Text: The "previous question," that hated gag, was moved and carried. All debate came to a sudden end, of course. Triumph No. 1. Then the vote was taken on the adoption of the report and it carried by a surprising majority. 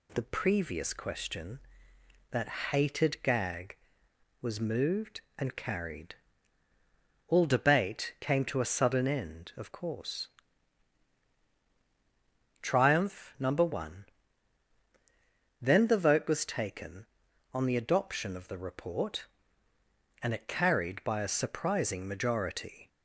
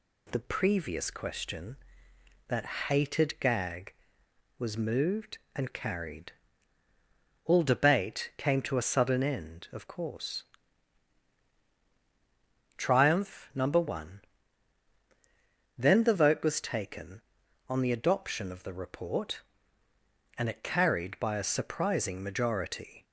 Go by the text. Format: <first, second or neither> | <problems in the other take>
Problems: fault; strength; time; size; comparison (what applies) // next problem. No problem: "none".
neither | pauses between "that" and "hated"; slight; the same in both